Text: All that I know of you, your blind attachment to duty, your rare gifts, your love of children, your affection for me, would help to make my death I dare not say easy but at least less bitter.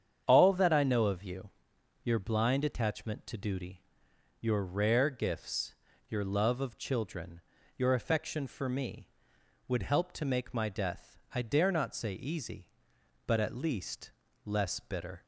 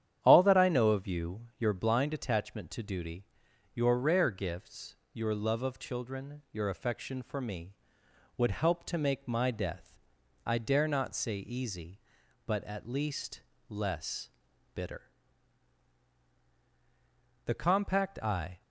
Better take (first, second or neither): first